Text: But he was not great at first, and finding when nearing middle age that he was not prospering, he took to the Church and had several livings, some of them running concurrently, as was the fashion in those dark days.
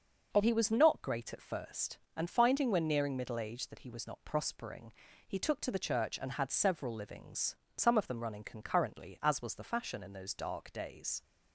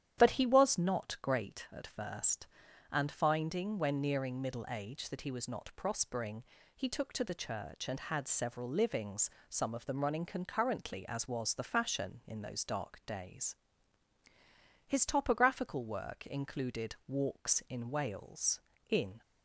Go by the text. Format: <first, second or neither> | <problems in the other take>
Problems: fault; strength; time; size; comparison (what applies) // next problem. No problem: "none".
first | starts louder than the rest; strong; until 1.2 s; 10.5 dB; noticeable in the first // goes on to say "His topographical work included Walks in Wales in"; strong; from 14.8 s on; 4.3 s long